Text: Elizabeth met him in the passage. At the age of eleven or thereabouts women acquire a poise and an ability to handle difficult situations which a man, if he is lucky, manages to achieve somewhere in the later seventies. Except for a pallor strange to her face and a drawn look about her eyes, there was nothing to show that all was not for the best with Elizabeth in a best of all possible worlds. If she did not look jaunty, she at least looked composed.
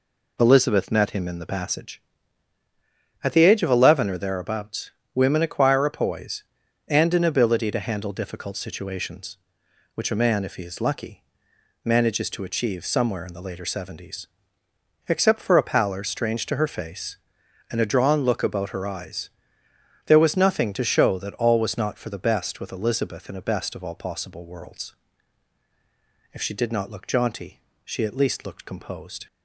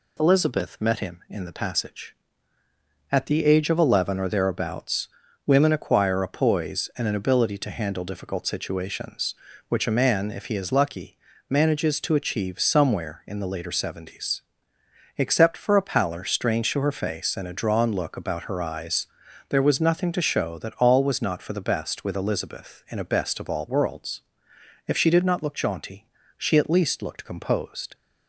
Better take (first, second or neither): first